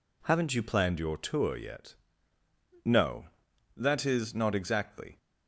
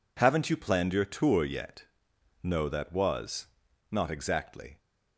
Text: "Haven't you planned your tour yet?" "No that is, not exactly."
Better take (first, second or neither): first